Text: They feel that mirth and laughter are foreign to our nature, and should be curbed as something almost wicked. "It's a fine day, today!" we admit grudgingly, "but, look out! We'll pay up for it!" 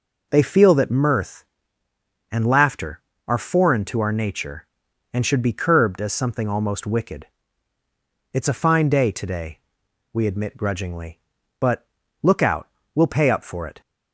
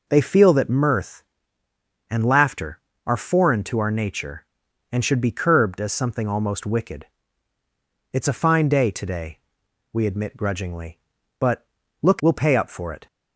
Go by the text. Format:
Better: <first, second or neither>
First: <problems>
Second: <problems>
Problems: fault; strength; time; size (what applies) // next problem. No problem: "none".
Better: first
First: none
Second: skips "out"; at 12.1 s